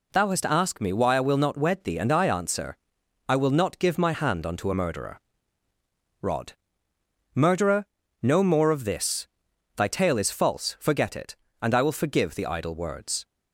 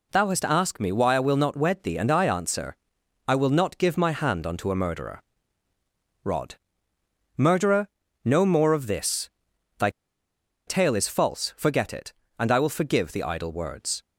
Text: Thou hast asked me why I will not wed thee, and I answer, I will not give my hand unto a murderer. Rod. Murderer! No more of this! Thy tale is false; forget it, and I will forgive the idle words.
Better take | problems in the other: first | pauses between "Thy" and "tale"; noticeable; at 9.8 s; 0.77 s long

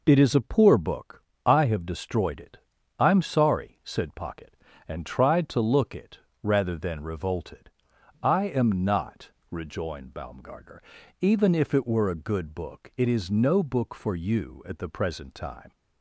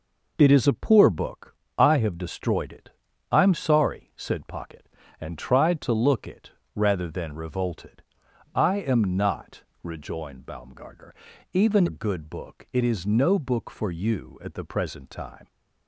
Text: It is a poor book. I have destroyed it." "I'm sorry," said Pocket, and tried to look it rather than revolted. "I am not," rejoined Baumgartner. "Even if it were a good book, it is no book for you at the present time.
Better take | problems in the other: first | pauses between "it" and "rather"; slight; at 6.4 s; 0.24 s long; slight in the first // skips "if it were"; at 11.8 s

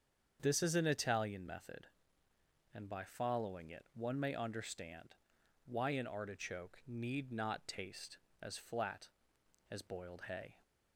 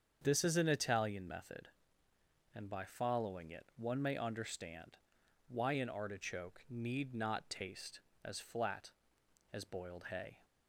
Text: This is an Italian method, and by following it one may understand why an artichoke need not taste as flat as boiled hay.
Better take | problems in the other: neither | starts louder than the rest; strong; the same in both // pauses between "understand" and "why"; noticeable; the same in both

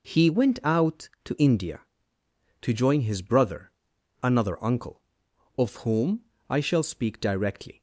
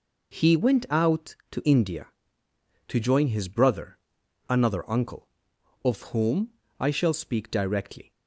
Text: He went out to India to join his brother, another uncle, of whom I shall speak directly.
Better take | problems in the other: neither | pauses between "whom" and "I"; slight; the same in both

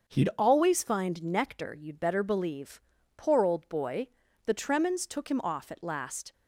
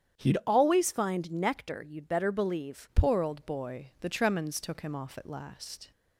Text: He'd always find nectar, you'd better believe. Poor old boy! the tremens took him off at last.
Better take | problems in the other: first | starts louder than the rest; strong; until 1.2 s; 9 dB; also in the first // changes voice at "Poor"; from 2.9 s on; 3.0 s long

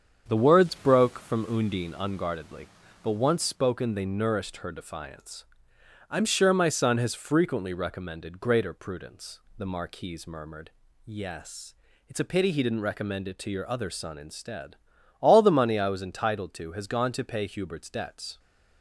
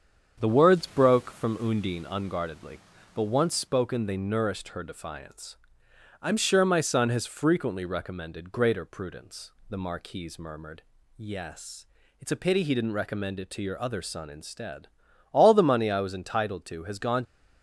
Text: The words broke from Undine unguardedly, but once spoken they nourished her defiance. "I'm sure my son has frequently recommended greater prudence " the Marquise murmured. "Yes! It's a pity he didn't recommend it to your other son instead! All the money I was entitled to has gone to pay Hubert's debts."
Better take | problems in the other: first | starts louder than the rest; strong; until 1.4 s; 7.5 dB; strong in the first // stops before "to pay Hubert's debts"; at 17.2 s

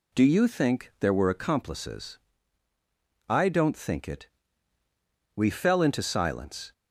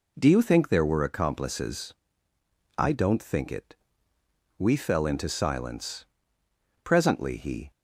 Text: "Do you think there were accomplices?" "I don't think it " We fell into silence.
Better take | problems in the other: first | goes on to say "Presently he"; noticeable; from 6.8 s on; 0.88 s long

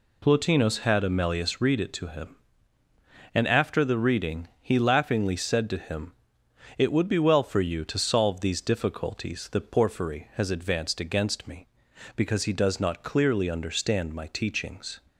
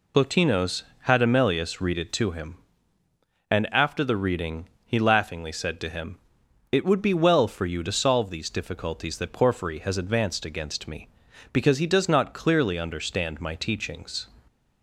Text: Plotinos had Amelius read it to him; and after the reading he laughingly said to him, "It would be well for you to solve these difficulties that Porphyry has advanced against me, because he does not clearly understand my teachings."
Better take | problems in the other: first | loses the start of "Plotinos"; at 0.1 s; 55 ms // pauses between "reading" and "he"; slight; at 4.6 s; 0.16 s long

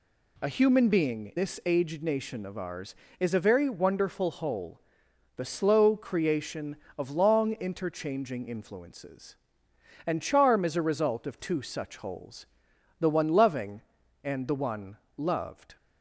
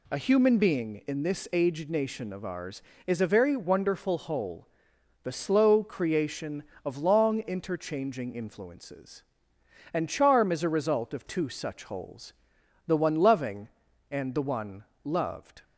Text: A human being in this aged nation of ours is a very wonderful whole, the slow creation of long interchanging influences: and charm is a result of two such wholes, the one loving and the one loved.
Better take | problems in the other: second | skips "in"; at 1.3 s // pauses between "one" and "loved"; slight; at 14.9 s; 0.20 s long; slight in the second

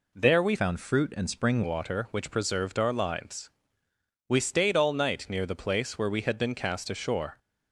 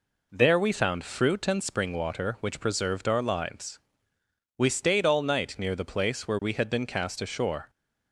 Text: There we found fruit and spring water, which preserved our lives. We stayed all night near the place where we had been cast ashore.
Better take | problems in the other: second | changes voice from "found" to "spring"; from 0.5 to 1.6 s; 1.1 s long

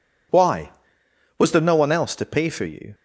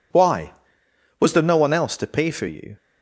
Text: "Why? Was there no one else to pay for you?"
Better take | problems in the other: neither | none

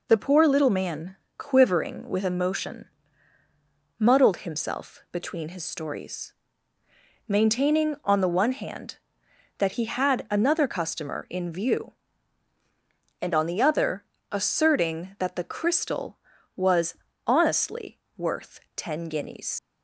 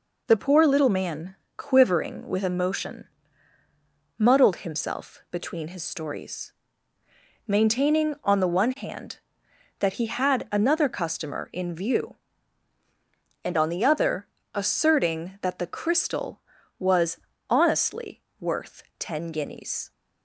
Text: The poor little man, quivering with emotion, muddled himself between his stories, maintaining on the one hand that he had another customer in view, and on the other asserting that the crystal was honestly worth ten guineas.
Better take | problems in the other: second | pauses between "other" and "asserting"; slight; at 14.0 s; 0.26 s long; slight in the second // pauses between "was" and "honestly"; slight; at 16.9 s; 0.30 s long; slight in the second // pauses between "honestly" and "worth"; slight; at 17.9 s; 0.20 s long; slight in the second // pauses between "worth" and "ten"; slight; at 18.5 s; 0.16 s long; slight in the second // leaves "guineas" unfinished; at 19.5 s; 100 ms

